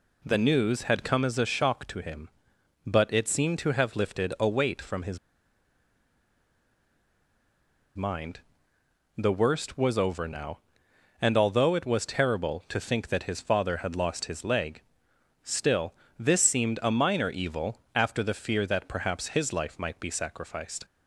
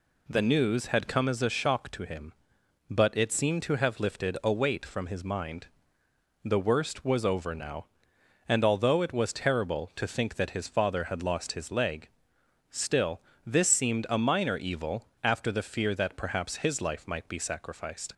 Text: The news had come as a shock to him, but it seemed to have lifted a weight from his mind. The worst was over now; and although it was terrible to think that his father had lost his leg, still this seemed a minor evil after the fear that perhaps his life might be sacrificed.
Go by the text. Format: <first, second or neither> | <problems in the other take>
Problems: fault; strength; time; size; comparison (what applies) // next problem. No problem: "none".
second | pauses between "his" and "mind"; strong; at 5.1 s; 2.7 s long // pauses between "still" and "this"; slight; at 15.9 s; 0.24 s long; slight in the second // pauses between "evil" and "after"; slight; at 17.7 s; 0.16 s long; slight in the second